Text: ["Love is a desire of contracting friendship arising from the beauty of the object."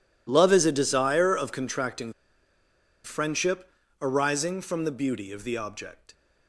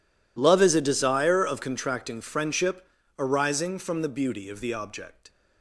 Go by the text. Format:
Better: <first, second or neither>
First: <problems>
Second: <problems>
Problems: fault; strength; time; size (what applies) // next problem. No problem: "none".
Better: second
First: pauses between "contracting" and "friendship"; noticeable; at 2.1 s; 0.92 s long // pauses between "friendship" and "arising"; slight; at 3.6 s; 0.32 s long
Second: pauses between "friendship" and "arising"; slight; at 2.8 s; 0.32 s long